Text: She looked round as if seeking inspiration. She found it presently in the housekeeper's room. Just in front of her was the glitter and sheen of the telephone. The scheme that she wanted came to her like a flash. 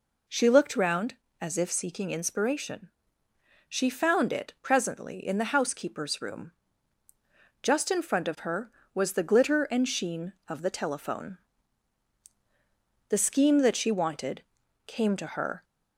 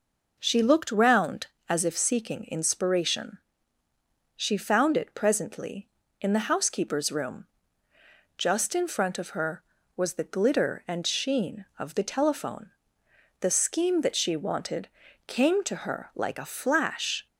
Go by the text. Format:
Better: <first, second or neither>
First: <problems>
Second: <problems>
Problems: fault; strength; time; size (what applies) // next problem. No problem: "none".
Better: second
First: pauses between "wanted" and "came"; at 14.4 s; 0.44 s long // stops before "like a flash"; at 15.6 s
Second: pauses between "wanted" and "came"; at 14.8 s; 0.38 s long